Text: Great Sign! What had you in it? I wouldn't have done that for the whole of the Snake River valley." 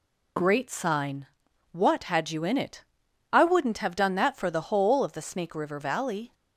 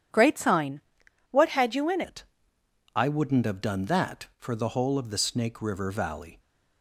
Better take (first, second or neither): first